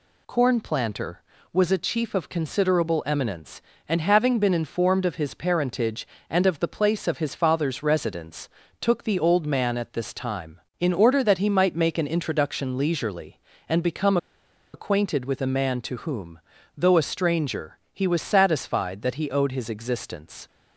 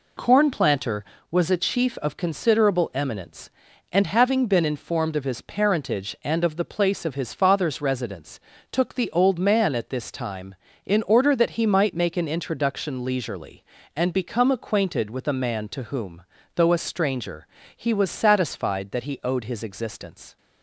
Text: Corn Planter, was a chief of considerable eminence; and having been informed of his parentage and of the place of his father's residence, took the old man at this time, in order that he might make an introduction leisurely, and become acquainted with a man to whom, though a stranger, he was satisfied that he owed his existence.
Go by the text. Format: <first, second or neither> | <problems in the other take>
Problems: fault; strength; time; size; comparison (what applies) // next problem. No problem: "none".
second | pauses between "become" and "acquainted"; noticeable; at 14.1 s; 0.57 s long